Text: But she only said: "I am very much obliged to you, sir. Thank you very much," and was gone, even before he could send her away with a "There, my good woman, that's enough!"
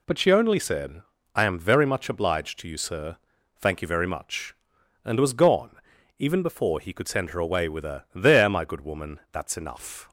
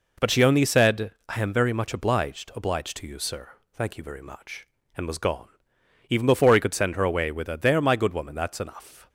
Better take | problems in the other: first | says "obliged" twice; at 2.5 s

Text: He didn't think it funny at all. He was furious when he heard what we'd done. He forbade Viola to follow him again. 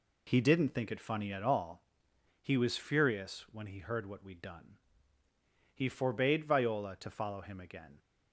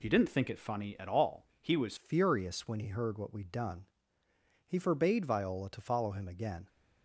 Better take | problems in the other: first | changes voice at "furious"; from 1.9 s on; 4.7 s long

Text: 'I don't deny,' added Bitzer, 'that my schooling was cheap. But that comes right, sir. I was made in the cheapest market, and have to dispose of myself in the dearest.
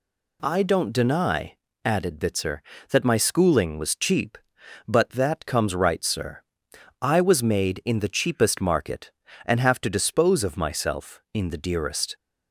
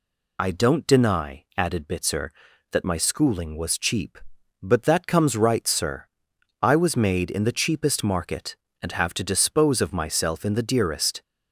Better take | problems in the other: first | loses the start of "I"; at 0.3 s; 25 ms

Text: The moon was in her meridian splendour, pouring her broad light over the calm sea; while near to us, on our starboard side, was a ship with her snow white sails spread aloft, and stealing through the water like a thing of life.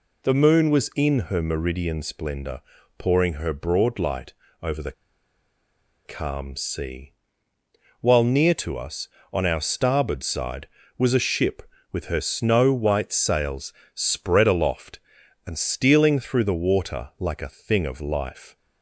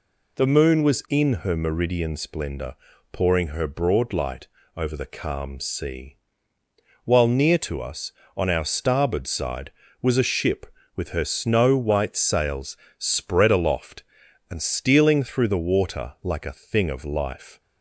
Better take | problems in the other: second | pauses between "light" and "over"; slight; at 4.3 s; 0.28 s long; slight in the second // pauses between "the" and "calm"; at 4.9 s; 1.1 s long // pauses between "sails" and "spread"; slight; at 13.7 s; 0.22 s long; slight in the second

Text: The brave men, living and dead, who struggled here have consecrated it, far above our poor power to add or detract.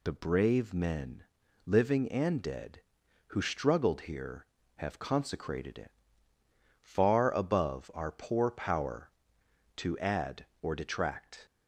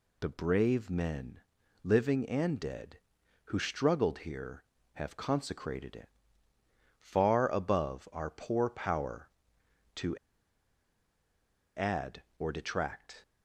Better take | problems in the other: first | pauses between "to" and "add"; strong; at 10.1 s; 1.6 s long

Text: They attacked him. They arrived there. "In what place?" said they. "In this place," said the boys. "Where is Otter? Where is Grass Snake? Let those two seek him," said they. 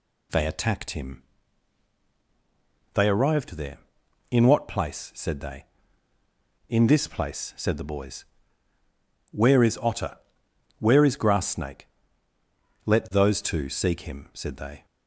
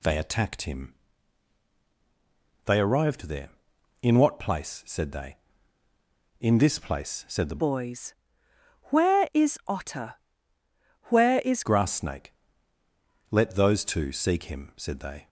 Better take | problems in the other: first | changes voice from "boys" to "is"; from 7.5 to 11.6 s; 4.1 s long

